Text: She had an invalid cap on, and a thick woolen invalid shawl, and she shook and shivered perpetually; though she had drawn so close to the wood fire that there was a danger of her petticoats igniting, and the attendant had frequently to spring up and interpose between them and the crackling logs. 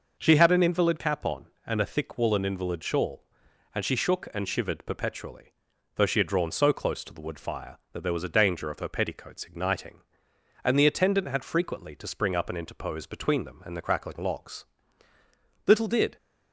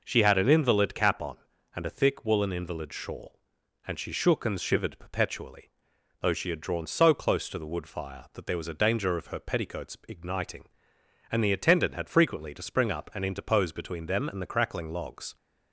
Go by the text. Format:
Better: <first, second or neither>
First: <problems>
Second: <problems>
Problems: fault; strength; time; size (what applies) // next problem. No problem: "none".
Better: second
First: goes on to say "Little did"; slight; from 15.6 s on; 0.48 s long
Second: none